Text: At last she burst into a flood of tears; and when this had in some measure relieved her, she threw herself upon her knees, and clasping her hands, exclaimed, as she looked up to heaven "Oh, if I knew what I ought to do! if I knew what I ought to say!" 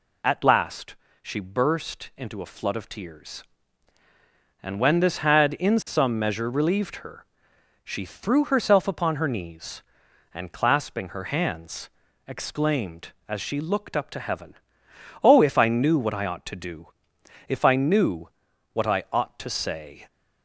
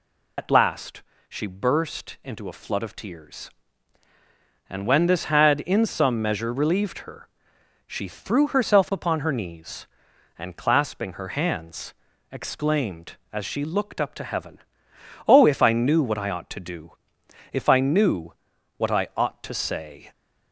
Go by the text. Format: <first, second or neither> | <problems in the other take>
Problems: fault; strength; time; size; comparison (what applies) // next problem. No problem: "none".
first | loses the start of "At"; at 0.3 s; 70 ms // pauses between "last" and "she"; slight; at 1.0 s; 0.28 s long; slight in the first // pauses between "heaven" and "Oh"; noticeable; at 14.5 s; 0.68 s long; noticeable in the first // pauses between "knew" and "what"; at 18.3 s; 0.44 s long; also in the first